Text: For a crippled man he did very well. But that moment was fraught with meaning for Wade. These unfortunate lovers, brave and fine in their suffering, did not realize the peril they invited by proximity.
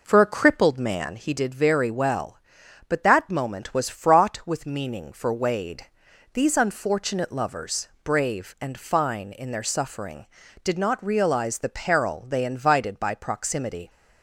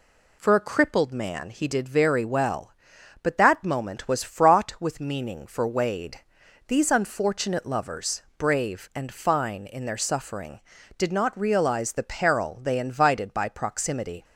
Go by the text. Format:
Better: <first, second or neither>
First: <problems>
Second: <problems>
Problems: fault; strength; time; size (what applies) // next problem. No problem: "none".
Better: second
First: starts louder than the rest; noticeable; until 1.3 s; 5 dB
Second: none